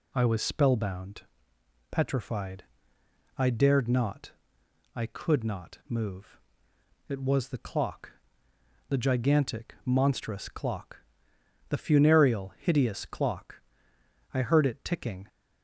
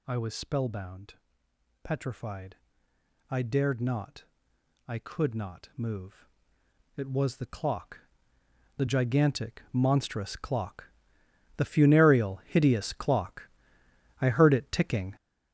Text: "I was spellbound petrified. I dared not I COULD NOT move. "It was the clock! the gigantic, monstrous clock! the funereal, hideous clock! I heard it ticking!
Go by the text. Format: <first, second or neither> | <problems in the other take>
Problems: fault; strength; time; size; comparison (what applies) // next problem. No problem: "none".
first | gets louder; strong; throughout; 7 dB // pauses between "spellbound" and "petrified"; noticeable; at 1.1 s; 0.68 s long; noticeable in the first // pauses between "not" and "I"; noticeable; at 4.2 s; 0.62 s long; noticeable in the first